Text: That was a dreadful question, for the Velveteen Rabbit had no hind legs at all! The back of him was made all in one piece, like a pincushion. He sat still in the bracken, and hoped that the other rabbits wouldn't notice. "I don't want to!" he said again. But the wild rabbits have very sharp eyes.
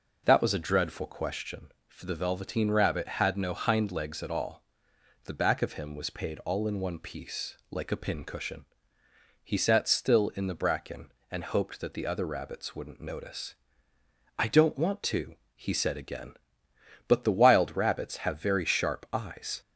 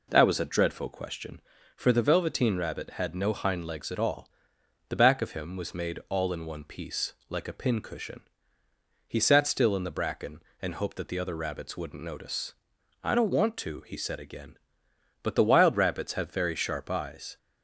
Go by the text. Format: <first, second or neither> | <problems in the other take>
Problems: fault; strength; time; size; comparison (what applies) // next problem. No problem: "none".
second | says "paid" for "made"; at 6.0 s